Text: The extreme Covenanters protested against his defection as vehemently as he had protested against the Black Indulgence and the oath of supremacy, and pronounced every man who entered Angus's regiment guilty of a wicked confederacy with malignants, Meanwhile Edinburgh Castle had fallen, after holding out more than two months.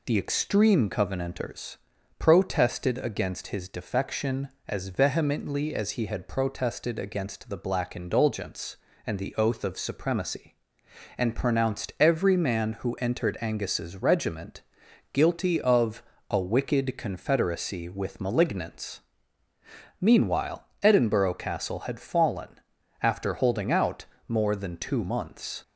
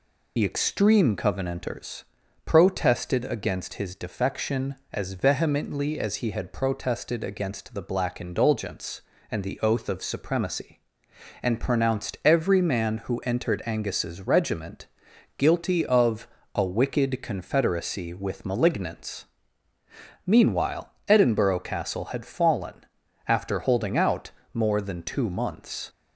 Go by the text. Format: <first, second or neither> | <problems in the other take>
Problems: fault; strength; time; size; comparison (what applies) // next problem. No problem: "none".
first | loses the start of "The"; at 0.3 s; 30 ms // pauses between "Covenanters" and "protested"; at 2.0 s; 0.40 s long; also in the first // pauses between "regiment" and "guilty"; noticeable; at 14.8 s; 0.52 s long; noticeable in the first // pauses between "of" and "a"; slight; at 16.2 s; 0.26 s long; slight in the first // pauses between "Meanwhile" and "Edinburgh"; slight; at 20.9 s; 0.16 s long; slight in the first // pauses between "out" and "more"; slight; at 24.2 s; 0.24 s long; slight in the first